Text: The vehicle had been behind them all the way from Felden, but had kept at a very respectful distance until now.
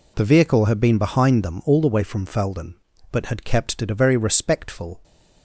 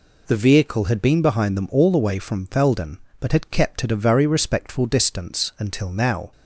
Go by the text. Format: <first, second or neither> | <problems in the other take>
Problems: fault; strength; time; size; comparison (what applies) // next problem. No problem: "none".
second | stops before "distance until now"; at 5.0 s